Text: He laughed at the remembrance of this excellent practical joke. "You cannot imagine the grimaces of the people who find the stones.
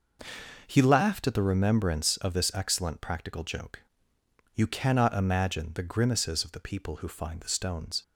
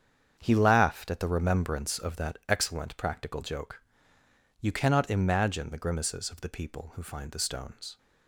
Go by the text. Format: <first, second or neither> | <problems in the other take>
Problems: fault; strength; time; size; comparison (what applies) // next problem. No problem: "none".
first | starts louder than the rest; strong; until 1.4 s; 8 dB // says "that" for "this"; at 2.1 s